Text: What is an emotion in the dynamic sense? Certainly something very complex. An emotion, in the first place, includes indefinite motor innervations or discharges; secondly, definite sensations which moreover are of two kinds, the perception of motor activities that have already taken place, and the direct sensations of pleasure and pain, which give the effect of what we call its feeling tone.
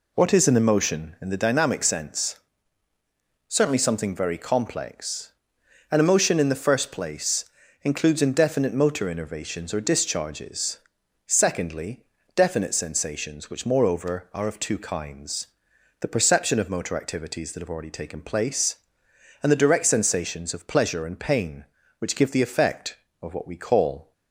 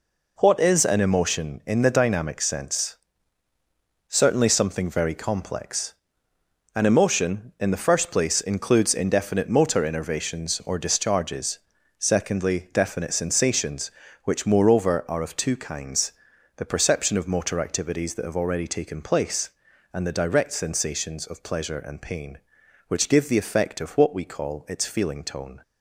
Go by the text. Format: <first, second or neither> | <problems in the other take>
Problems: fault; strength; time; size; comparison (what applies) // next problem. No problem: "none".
second | stops before "its feeling tone"; at 24.1 s